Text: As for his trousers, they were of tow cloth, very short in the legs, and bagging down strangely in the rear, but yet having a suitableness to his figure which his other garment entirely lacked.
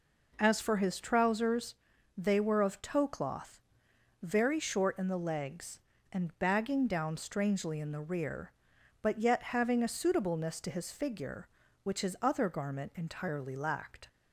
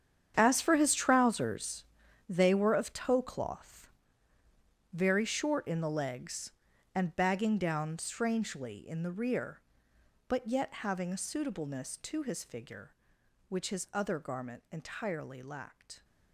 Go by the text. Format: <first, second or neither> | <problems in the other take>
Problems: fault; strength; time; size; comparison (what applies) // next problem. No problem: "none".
first | gets quieter; strong; throughout; 14 dB